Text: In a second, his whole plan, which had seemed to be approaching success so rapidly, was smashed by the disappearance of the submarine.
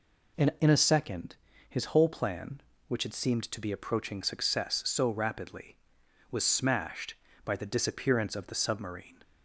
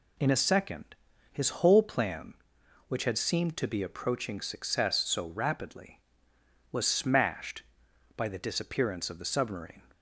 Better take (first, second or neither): second